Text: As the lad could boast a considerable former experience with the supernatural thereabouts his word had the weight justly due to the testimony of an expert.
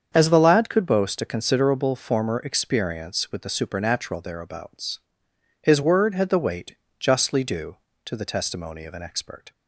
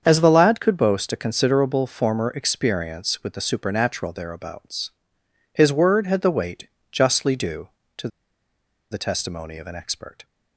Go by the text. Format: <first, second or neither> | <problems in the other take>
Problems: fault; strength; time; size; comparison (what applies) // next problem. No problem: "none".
first | starts louder than the rest; strong; until 1.0 s; 7.5 dB; strong in the first // pauses between "thereabouts" and "his"; noticeable; at 4.8 s; 0.64 s long; noticeable in the first // pauses between "weight" and "justly"; slight; at 6.6 s; 0.24 s long; slight in the first // pauses between "to" and "the"; noticeable; at 8.0 s; 0.83 s long